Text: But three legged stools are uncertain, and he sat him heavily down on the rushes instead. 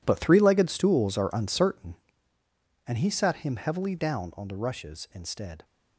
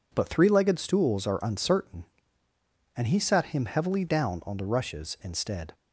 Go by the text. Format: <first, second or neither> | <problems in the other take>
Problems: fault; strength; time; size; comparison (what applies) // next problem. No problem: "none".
second | gets quieter; strong; throughout; 14.5 dB